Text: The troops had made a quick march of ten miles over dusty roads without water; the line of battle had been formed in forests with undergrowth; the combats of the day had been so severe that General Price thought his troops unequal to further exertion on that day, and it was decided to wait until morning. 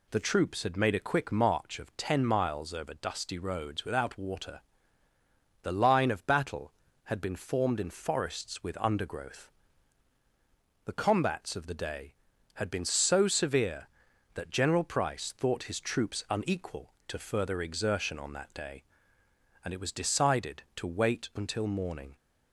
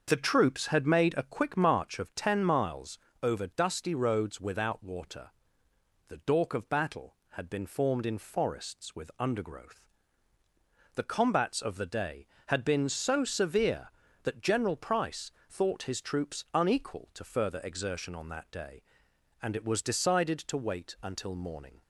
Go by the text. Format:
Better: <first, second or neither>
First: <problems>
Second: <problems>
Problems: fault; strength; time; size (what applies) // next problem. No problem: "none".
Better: first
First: none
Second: starts louder than the rest; until 1.0 s; 6.5 dB // pauses between "miles" and "over"; slight; at 2.9 s; 0.24 s long // says "dork" for "line"; at 6.1 s // pauses between "Price" and "thought"; slight; at 15.2 s; 0.20 s long